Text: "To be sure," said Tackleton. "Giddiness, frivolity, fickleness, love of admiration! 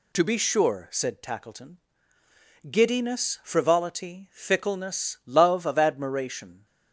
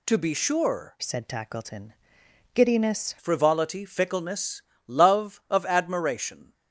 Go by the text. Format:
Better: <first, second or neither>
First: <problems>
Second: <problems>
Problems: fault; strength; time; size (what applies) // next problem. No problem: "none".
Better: first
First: none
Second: changes voice from "said" to "Giddiness"; from 1.0 to 3.1 s; 2.1 s long